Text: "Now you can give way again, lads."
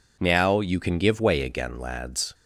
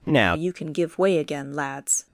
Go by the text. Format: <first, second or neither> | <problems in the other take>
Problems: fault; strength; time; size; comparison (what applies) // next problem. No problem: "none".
first | changes voice at "you"; from 0.3 s on; 1.7 s long